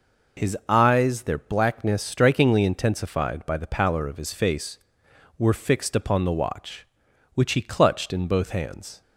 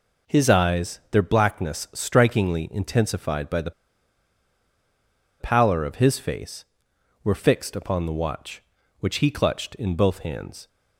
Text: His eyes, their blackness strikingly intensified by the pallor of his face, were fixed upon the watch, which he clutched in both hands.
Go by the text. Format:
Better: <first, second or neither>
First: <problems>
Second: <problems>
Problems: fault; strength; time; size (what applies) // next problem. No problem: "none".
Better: first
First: none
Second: pauses between "the" and "pallor"; strong; at 3.7 s; 1.6 s long